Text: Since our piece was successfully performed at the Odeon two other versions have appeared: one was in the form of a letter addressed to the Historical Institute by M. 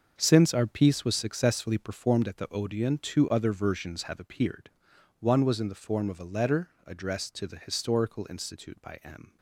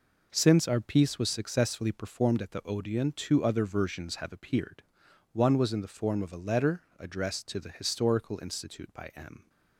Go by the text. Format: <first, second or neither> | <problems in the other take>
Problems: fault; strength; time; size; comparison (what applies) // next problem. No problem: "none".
second | gets quieter; strong; throughout; 12 dB // pauses between "letter" and "addressed"; slight; at 6.6 s; 0.18 s long; slight in the second